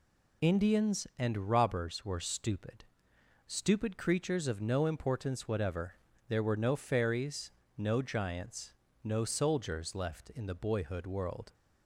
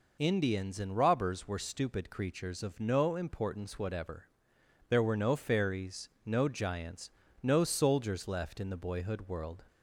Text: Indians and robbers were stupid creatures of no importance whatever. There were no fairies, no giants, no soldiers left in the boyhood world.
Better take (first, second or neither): second